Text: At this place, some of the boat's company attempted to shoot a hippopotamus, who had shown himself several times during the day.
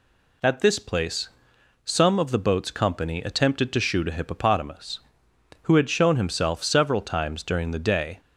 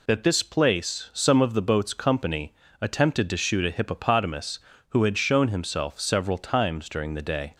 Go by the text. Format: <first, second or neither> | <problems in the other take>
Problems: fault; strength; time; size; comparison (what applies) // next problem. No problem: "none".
first | says "That" for "At"; at 0.0 s // pauses between "company" and "attempted"; slight; at 2.5 s; 0.28 s long